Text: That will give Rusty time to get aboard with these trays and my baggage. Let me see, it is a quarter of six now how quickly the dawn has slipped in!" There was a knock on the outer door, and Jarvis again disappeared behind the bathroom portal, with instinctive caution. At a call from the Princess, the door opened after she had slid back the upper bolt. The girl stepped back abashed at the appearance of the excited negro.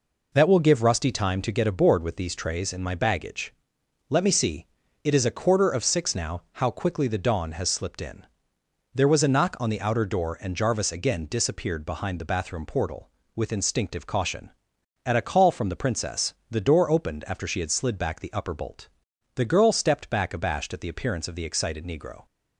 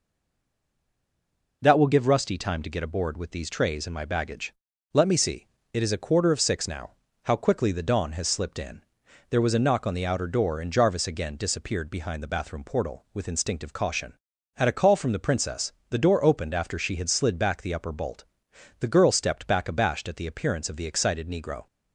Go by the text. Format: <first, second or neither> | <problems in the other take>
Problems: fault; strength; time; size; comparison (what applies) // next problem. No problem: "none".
first | stays silent before the first word; noticeable; until 1.6 s; 1.6 s long // pauses between "now" and "how"; slight; at 6.9 s; 0.28 s long